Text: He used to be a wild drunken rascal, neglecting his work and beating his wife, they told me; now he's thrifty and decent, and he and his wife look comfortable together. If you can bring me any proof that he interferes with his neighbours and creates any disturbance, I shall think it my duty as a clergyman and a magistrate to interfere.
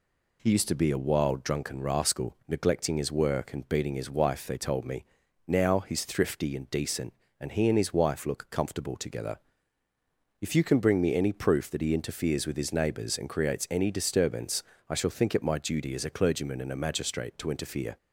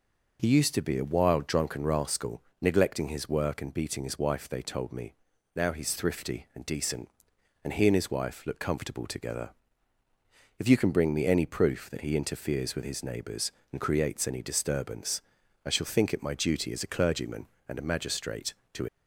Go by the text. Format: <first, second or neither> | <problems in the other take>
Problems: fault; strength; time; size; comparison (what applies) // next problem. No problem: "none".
first | stops before "interfere"; at 18.8 s